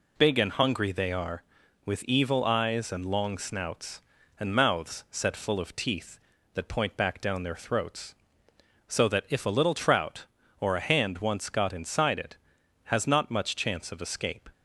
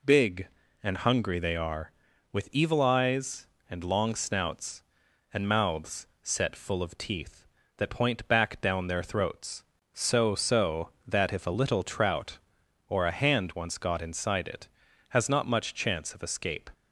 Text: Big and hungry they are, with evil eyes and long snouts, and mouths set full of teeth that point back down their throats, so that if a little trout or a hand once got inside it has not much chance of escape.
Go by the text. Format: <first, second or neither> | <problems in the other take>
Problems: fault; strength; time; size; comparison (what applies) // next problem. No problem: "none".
first | pauses between "mouths" and "set"; slight; at 6.0 s; 0.16 s long // says "so" twice; at 10.3 s